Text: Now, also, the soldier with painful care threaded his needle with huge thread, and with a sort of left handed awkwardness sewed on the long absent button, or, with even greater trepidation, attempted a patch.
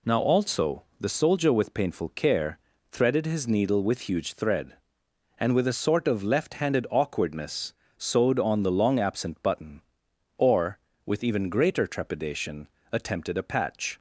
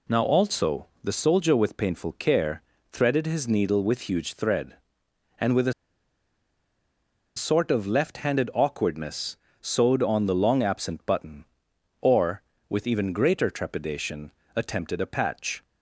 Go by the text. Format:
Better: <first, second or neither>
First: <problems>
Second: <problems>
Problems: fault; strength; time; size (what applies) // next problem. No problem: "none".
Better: first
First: pauses between "care" and "threaded"; slight; at 2.5 s; 0.35 s long // pauses between "awkwardness" and "sewed"; slight; at 7.7 s; 0.26 s long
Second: pauses between "care" and "threaded"; slight; at 2.6 s; 0.32 s long // pauses between "a" and "sort"; strong; at 5.7 s; 1.6 s long // pauses between "awkwardness" and "sewed"; slight; at 9.3 s; 0.26 s long